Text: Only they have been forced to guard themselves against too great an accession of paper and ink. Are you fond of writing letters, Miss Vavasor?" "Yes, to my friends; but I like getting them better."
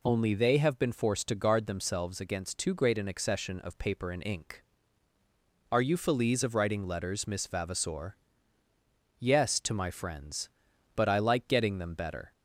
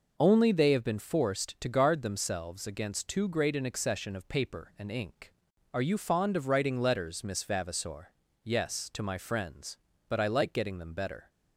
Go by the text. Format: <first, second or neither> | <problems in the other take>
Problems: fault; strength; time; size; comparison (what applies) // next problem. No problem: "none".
second | says "feliz" for "fond"; at 5.9 s